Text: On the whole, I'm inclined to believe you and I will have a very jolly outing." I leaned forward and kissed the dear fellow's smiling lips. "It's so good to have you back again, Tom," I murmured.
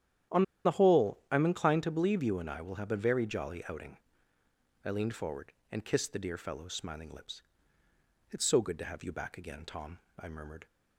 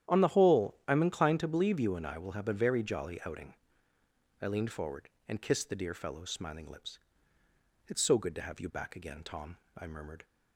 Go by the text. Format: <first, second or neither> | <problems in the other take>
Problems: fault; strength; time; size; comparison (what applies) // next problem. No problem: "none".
second | starts louder than the rest; strong; until 1.6 s; 10 dB; strong in the second // pauses between "On" and "the"; slight; at 0.4 s; 0.21 s long